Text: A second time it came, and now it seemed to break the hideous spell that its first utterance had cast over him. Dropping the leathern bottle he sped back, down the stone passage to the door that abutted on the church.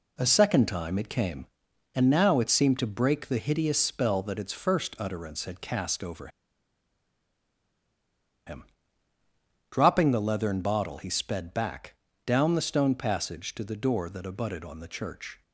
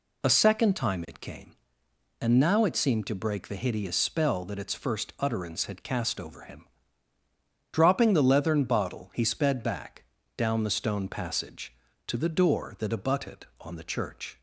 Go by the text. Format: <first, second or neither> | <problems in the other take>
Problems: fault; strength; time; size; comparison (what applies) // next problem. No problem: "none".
second | pauses between "over" and "him"; strong; at 6.2 s; 2.1 s long